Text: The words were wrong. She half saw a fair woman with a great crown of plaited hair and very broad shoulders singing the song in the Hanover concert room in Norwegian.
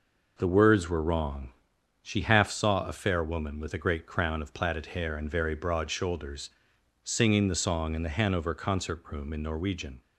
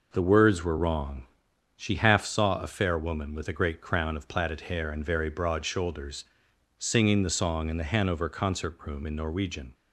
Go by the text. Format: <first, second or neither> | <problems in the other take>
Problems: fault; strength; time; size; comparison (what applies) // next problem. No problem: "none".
neither | pauses between "shoulders" and "singing"; noticeable; the same in both